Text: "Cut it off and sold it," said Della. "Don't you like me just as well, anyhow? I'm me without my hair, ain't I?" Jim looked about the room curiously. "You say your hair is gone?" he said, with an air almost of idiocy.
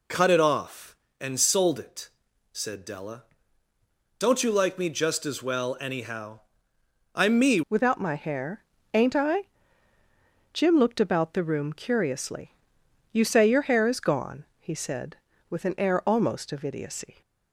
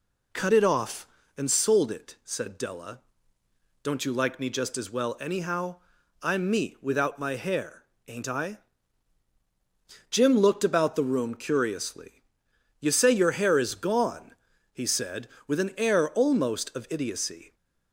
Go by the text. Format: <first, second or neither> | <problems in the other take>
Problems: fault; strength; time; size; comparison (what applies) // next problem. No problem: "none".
second | changes voice at "without"; from 7.6 s on; 9.6 s long